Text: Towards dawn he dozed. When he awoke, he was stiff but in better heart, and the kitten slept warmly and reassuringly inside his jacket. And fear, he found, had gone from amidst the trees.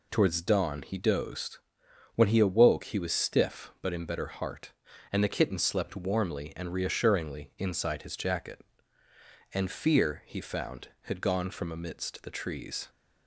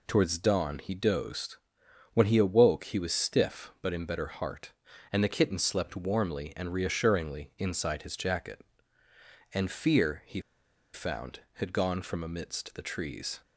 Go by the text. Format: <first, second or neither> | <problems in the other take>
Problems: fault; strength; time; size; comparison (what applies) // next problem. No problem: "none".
first | pauses between "he" and "found"; noticeable; at 10.4 s; 0.52 s long